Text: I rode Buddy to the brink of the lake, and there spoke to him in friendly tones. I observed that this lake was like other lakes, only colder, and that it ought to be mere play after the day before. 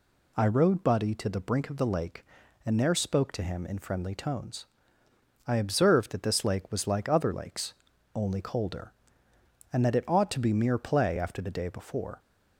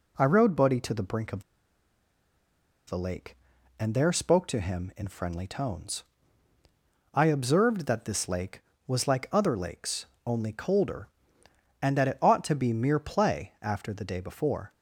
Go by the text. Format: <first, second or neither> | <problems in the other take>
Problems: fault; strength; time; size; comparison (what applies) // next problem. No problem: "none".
first | pauses between "of" and "the"; strong; at 1.4 s; 1.4 s long